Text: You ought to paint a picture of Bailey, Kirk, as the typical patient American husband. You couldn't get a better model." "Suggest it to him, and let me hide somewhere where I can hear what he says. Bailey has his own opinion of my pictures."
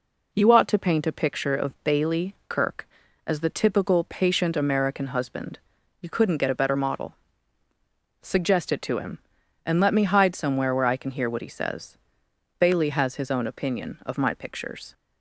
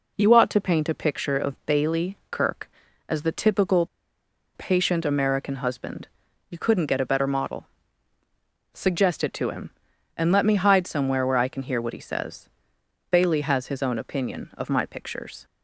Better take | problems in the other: first | pauses between "typical" and "patient"; noticeable; at 3.8 s; 0.68 s long

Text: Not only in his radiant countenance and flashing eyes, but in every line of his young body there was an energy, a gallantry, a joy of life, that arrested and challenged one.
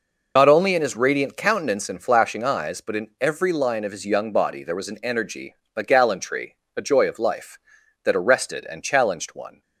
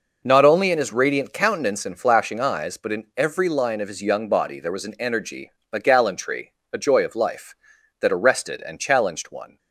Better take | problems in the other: second | loses the start of "Not"; at 0.3 s; 70 ms

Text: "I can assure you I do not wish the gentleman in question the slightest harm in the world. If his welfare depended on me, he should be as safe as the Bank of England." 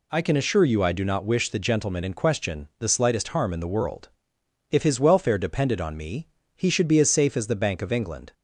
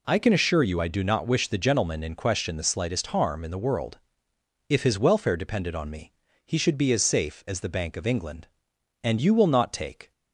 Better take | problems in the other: first | goes on to say "And you will not take"; noticeable; from 9.0 s on; 1.0 s long

